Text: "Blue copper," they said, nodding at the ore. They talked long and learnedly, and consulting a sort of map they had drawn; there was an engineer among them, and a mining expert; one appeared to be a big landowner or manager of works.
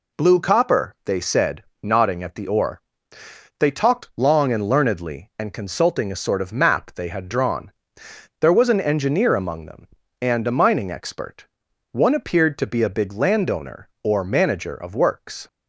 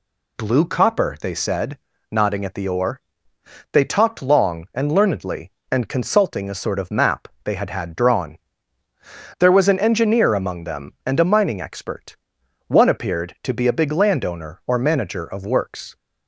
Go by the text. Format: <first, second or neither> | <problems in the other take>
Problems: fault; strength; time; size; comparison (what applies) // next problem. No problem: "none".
first | pauses between "map" and "they"; slight; at 7.2 s; 0.18 s long // says "had" twice; at 7.7 s